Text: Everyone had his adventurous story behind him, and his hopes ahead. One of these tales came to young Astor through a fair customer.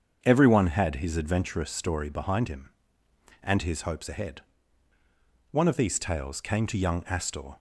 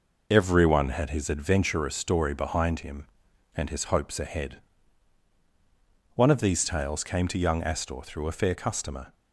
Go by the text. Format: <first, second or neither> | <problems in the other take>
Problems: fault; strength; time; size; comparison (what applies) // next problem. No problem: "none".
second | starts louder than the rest; strong; until 1.2 s; 7 dB // stops before "through a fair customer"; at 7.5 s